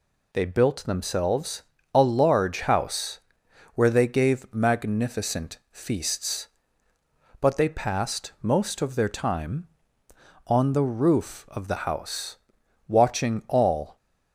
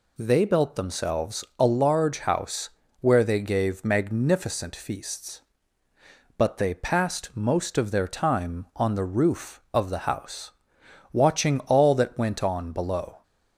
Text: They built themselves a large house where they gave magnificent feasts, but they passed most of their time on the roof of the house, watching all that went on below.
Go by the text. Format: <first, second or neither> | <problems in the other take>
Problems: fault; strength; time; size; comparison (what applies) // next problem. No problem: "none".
second | pauses between "themselves" and "a"; slight; at 1.6 s; 0.30 s long // pauses between "house" and "where"; noticeable; at 3.2 s; 0.54 s long; slight in the second // stops before "that went on below"; at 13.9 s